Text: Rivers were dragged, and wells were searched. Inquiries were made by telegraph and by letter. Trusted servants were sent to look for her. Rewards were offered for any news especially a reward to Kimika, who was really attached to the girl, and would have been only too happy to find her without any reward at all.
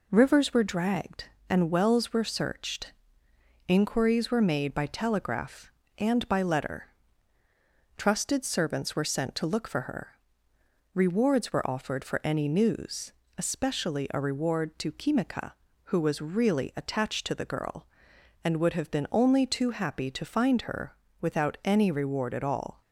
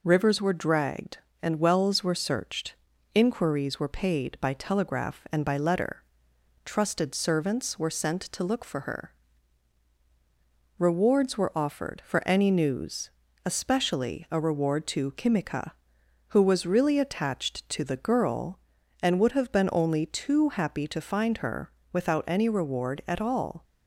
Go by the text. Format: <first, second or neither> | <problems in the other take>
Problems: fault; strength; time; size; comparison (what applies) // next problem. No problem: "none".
first | says "paid" for "made"; at 3.8 s // pauses between "news" and "especially"; slight; at 13.0 s; 0.36 s long; slight in the first // pauses between "her" and "without"; slight; at 21.7 s; 0.20 s long; slight in the first